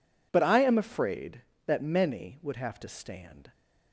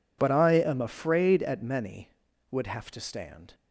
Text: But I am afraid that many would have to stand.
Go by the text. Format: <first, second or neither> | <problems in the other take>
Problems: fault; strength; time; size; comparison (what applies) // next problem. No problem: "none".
first | says "at" for "that"; at 1.4 s